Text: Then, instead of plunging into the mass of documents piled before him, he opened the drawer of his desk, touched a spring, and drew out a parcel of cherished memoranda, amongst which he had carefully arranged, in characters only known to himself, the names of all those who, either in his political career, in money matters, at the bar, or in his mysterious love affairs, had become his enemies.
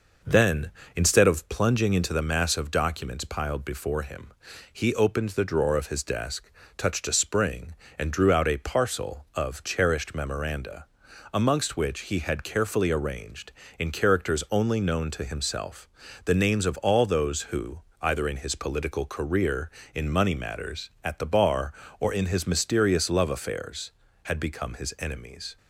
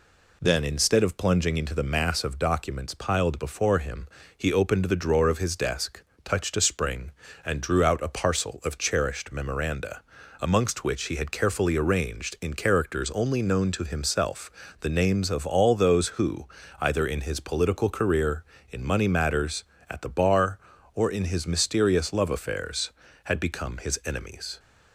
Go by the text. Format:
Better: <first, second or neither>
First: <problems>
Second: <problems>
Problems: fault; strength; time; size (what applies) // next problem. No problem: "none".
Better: second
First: starts louder than the rest; noticeable; until 1.4 s; 5.5 dB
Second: none